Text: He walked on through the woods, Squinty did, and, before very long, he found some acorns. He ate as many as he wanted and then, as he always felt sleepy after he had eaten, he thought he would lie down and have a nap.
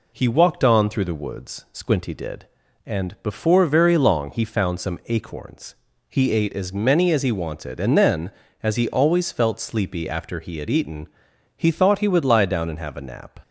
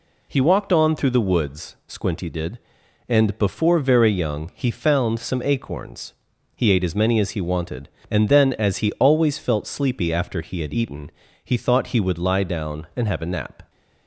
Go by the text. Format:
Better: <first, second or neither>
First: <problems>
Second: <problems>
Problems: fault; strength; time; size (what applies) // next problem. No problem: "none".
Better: first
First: none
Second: says "young" for "long"; at 4.1 s